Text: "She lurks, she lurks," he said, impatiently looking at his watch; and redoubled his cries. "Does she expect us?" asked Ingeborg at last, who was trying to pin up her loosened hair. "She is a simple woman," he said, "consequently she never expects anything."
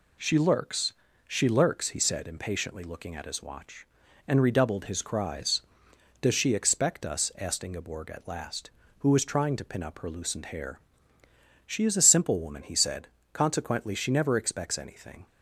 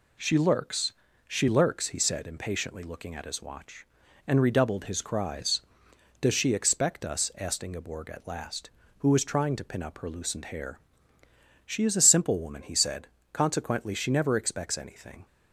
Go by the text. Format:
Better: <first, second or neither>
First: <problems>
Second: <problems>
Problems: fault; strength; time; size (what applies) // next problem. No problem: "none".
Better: neither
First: none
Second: none